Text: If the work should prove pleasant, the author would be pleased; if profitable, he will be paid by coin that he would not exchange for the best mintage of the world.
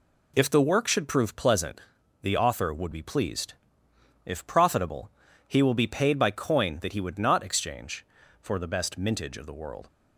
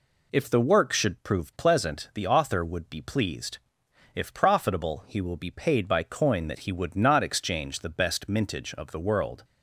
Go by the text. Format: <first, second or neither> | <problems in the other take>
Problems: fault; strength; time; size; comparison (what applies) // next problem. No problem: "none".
first | skips "for"; at 7.7 s